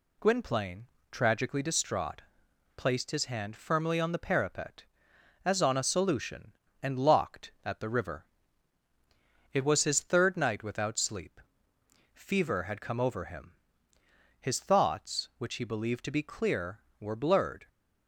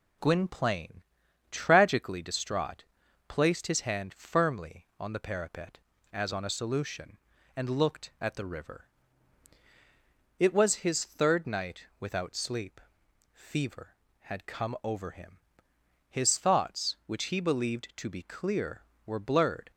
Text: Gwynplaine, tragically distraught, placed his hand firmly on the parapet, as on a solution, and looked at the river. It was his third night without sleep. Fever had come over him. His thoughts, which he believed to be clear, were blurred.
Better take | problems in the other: second | says "locked" for "looked"; at 6.9 s

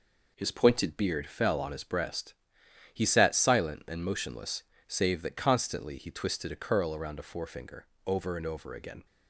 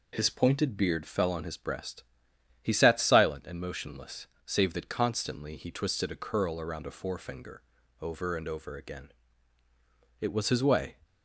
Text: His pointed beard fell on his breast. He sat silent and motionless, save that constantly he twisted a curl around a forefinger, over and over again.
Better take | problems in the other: first | goes on to say "It was his way"; noticeable; from 10.1 s on; 0.80 s long

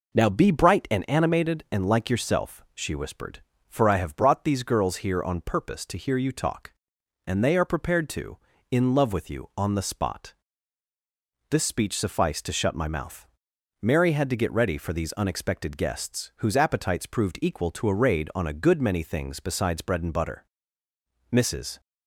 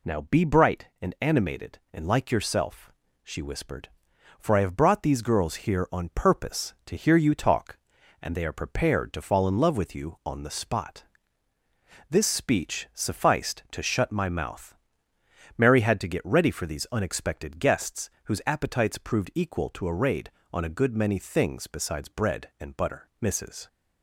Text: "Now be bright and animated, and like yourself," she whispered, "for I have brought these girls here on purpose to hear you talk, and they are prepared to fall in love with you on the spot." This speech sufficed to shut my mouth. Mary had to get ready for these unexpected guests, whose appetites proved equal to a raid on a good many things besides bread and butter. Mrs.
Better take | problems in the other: second | skips "fall"; at 8.5 s

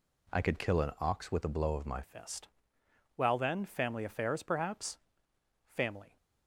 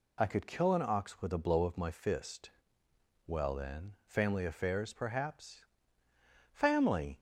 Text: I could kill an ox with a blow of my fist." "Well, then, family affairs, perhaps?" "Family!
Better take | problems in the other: second | changes voice at "fist"; from 2.0 s on; 4.1 s long

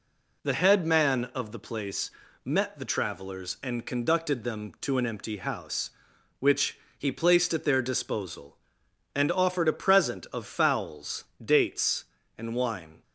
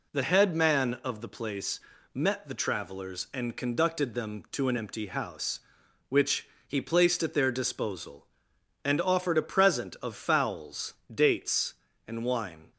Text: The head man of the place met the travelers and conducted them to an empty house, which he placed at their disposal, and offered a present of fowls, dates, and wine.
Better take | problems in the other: neither | pauses between "place" and "met"; slight; the same in both // pauses between "which" and "he"; slight; the same in both

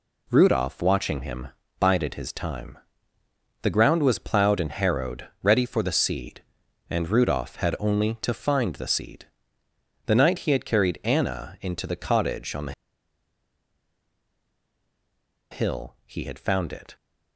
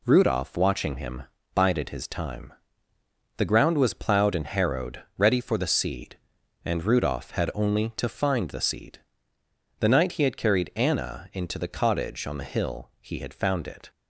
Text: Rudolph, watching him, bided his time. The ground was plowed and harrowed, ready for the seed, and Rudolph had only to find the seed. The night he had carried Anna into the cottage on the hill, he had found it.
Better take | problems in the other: second | pauses between "the" and "hill"; strong; at 12.7 s; 2.7 s long

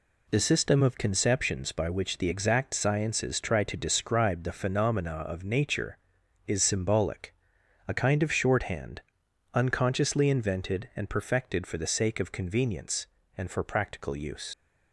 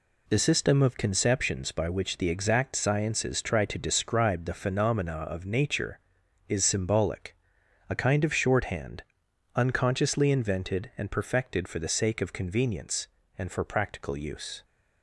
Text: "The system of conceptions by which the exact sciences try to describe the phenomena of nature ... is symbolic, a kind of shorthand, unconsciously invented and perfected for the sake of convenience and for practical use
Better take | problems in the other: second | leaves "use" unfinished; at 14.5 s; 100 ms

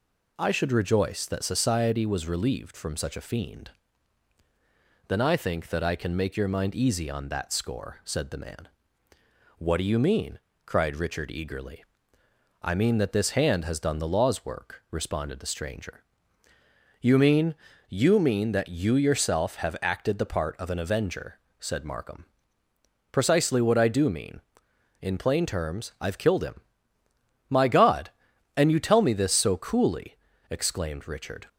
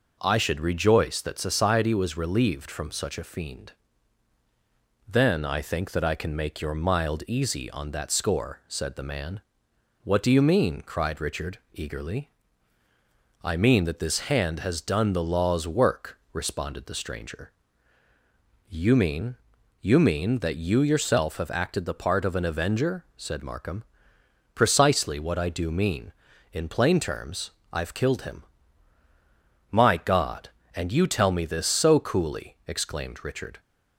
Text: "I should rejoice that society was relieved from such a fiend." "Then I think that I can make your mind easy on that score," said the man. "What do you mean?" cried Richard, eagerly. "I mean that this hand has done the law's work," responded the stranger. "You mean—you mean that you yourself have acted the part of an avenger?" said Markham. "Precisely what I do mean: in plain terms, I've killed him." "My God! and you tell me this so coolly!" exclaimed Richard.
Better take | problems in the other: first | says "mild" for "mind"; at 6.7 s

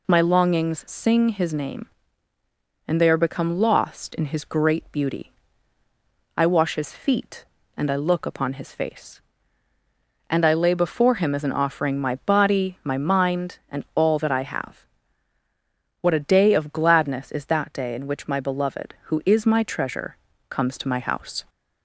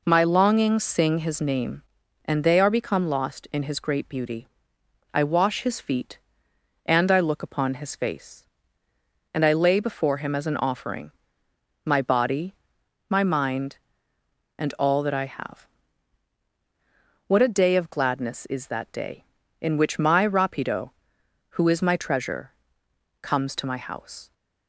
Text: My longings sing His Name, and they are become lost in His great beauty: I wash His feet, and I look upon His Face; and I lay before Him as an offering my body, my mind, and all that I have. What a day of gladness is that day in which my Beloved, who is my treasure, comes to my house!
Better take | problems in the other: first | pauses between "offering" and "my"; noticeable; at 11.1 s; 0.72 s long // says "Rapido" for "Beloved"; at 20.2 s

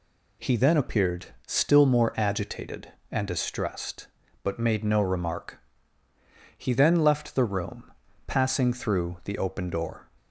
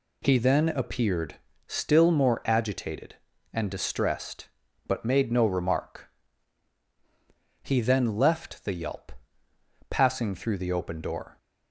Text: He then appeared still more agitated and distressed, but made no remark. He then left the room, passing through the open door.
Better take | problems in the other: first | pauses between "appeared" and "still"; slight; at 1.3 s; 0.32 s long; slight in the first // says "yelp" for "room"; at 8.7 s

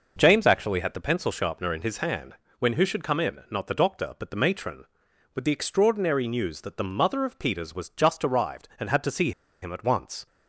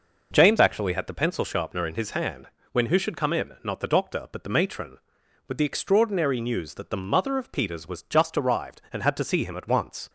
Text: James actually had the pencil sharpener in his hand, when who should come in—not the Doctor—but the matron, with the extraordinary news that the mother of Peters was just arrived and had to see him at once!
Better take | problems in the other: second | pauses between "see" and "him"; slight; at 9.3 s; 0.31 s long

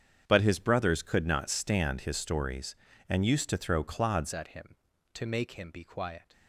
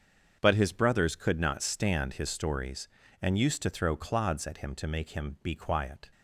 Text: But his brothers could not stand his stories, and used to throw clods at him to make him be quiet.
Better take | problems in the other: second | starts louder than the rest; strong; until 1.2 s; 8 dB; also in the second // changes voice at "at"; from 4.3 s on; 2.0 s long

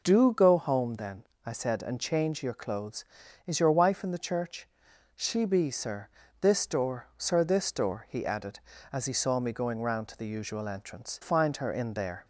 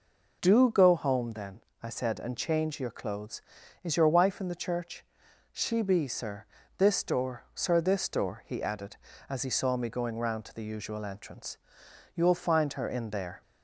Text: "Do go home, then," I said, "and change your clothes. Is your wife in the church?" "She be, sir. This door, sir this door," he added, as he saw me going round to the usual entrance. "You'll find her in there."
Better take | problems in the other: second | skips "You'll"; at 11.2 s

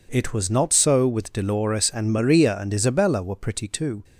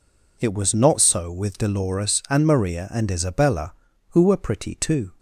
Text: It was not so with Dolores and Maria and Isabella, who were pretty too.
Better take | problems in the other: second | skips "who"; at 3.2 s

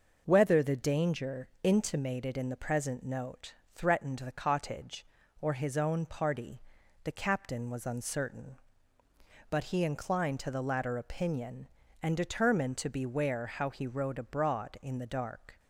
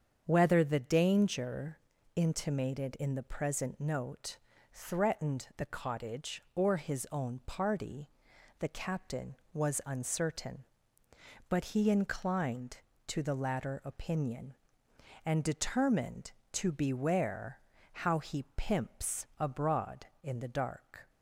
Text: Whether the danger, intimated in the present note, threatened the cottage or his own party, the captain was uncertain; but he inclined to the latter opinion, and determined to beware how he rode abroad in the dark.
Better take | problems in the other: first | starts louder than the rest; strong; until 1.2 s; 7.5 dB // pauses between "beware" and "how"; slight; at 17.5 s; 0.32 s long // says "pimps" for "rode"; at 18.5 s

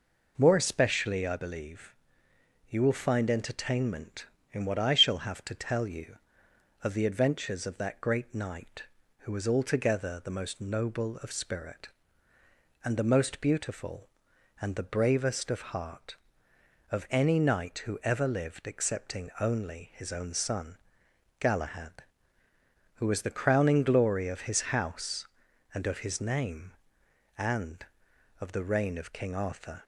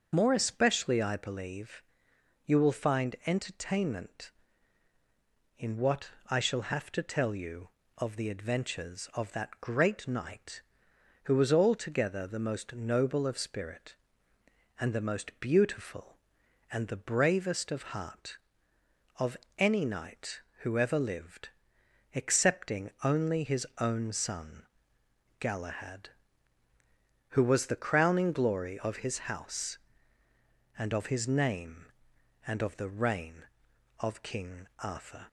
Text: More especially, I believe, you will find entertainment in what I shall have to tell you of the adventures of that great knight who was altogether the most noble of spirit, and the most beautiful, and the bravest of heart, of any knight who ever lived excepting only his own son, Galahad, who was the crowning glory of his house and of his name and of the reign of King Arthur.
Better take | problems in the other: first | loses the start of "More"; at 0.1 s; 65 ms // starts louder than the rest; until 1.1 s; 6 dB // pauses between "what" and "I"; slight; at 6.1 s; 0.18 s long // pauses between "of" and "any"; slight; at 19.3 s; 0.22 s long // pauses between "lived" and "excepting"; noticeable; at 21.4 s; 0.66 s long

